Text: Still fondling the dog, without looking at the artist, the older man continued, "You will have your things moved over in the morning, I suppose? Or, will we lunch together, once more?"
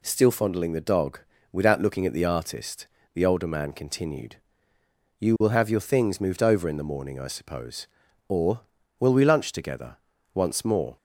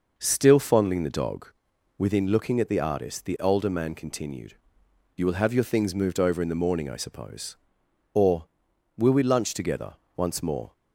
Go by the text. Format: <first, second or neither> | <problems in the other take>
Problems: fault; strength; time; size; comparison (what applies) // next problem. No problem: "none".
first | says "within" for "without"; at 1.9 s